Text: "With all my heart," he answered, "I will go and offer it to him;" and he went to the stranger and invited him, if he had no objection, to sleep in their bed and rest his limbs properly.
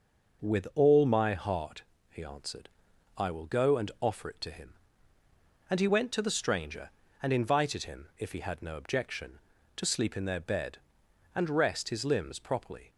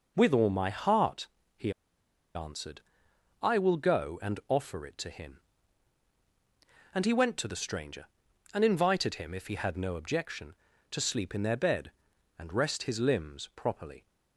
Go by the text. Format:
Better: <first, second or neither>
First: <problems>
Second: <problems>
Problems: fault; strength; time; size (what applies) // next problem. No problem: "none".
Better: first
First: none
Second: pauses between "he" and "answered"; noticeable; at 1.7 s; 0.64 s long